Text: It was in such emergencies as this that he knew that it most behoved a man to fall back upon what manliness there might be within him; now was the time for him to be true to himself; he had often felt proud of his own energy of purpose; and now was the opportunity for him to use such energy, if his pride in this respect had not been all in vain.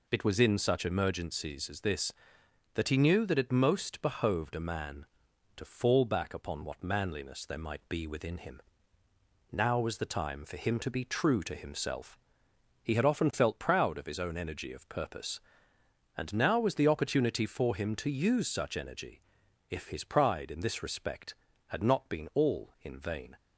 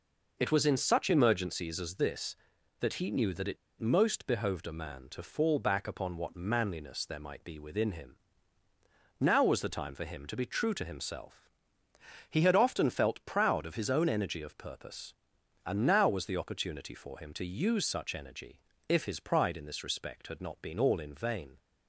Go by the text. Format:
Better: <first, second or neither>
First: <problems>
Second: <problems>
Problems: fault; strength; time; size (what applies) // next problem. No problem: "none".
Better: first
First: none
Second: pauses between "it" and "most"; slight; at 3.5 s; 0.23 s long